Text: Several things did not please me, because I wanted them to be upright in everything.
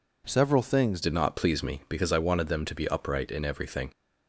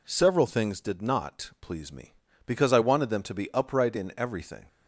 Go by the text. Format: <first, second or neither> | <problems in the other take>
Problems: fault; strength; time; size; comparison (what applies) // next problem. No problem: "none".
second | changes voice at "did"; from 1.0 s on; 2.9 s long